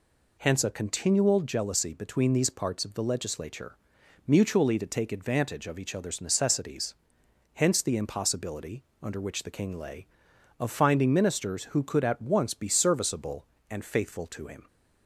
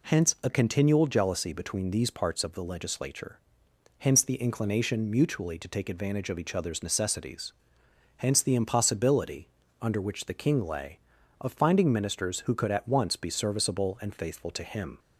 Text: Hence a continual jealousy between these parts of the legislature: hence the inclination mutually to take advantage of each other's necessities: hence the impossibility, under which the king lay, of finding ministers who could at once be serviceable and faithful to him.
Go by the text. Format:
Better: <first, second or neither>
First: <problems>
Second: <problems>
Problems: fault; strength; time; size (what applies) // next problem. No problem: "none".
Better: second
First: skips "hence the inclination"; at 4.0 s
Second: none